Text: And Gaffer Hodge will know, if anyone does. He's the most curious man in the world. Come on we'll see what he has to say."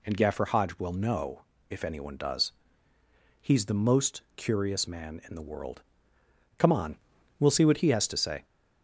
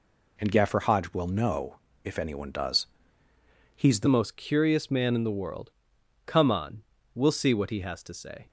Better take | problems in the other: first | changes voice at "most"; from 4.0 s on; 4.4 s long // pauses between "on" and "we'll"; slight; at 6.8 s; 0.34 s long; also in the first

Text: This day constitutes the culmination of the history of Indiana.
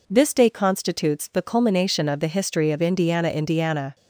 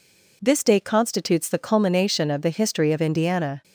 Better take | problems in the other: second | says "Indiana" twice; at 3.2 s

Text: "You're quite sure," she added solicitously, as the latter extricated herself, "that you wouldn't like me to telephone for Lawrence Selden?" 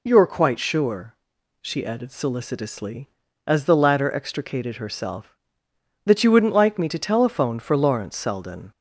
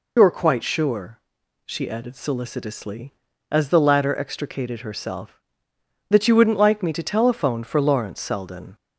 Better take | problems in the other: first | loses the start of "You're"; at 0.1 s; 75 ms

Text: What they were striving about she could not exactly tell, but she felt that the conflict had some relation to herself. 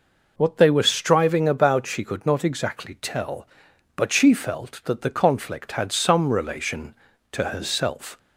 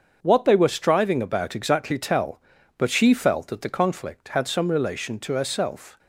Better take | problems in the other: first | starts louder than the rest; until 1.2 s; 7 dB // skips "she could not"; at 1.5 s

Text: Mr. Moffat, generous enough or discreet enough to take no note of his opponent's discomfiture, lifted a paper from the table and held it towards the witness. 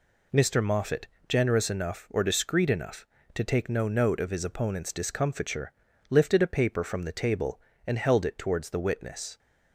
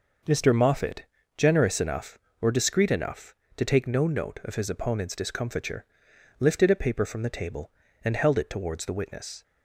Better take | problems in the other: neither | none

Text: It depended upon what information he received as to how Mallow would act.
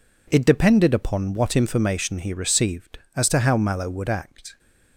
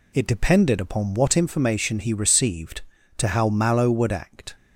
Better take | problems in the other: first | skips "as"; at 2.9 s

